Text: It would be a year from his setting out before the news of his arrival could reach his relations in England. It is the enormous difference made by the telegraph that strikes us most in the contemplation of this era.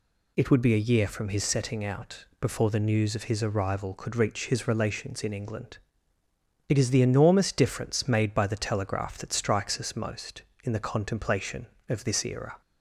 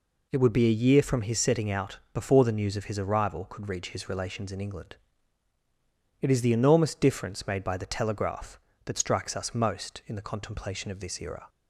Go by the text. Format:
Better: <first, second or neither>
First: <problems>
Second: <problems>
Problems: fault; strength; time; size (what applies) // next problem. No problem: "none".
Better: neither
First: none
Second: none